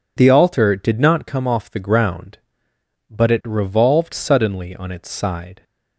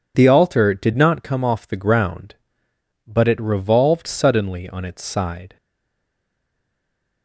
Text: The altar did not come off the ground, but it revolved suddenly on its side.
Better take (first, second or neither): first